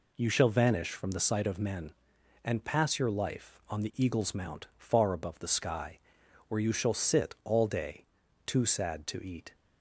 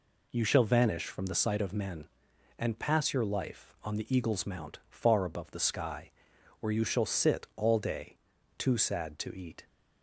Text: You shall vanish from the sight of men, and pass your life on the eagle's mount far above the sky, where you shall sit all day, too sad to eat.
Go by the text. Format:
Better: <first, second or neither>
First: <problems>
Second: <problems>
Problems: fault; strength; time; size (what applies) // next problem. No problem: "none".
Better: neither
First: none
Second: none